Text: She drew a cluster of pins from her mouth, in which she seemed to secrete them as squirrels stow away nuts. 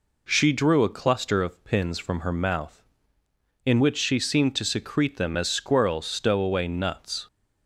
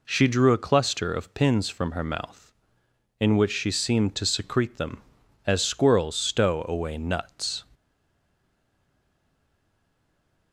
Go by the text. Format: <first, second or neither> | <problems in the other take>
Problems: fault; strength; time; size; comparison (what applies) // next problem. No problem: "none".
first | stays silent after the last word; strong; from 7.7 s on; 2.8 s long